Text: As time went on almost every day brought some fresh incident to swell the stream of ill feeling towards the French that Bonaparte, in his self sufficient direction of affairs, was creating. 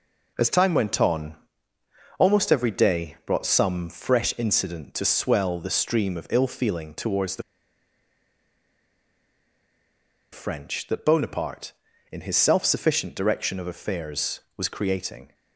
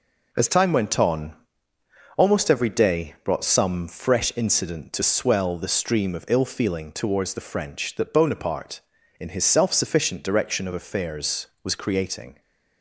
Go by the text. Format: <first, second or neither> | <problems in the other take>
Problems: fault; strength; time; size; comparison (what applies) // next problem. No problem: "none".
second | pauses between "on" and "almost"; noticeable; at 1.3 s; 0.82 s long; noticeable in the second // pauses between "the" and "French"; strong; at 7.4 s; 2.9 s long